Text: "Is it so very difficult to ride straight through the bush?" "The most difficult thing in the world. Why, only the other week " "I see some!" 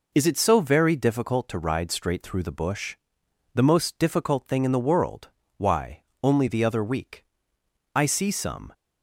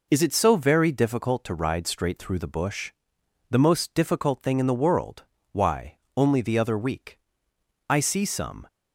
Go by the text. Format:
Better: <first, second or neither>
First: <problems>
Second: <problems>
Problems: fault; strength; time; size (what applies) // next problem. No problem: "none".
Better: neither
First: none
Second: none